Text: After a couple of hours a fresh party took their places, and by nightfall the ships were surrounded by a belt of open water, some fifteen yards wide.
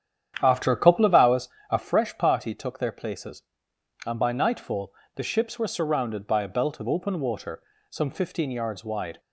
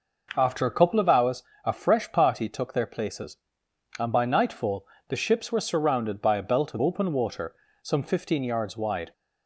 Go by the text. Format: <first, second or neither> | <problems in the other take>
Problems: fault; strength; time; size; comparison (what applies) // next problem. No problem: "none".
second | starts louder than the rest; strong; until 2.0 s; 9.5 dB // pauses between "hours" and "a"; slight; at 1.4 s; 0.24 s long; slight in the second // pauses between "nightfall" and "the"; slight; at 4.9 s; 0.22 s long; slight in the second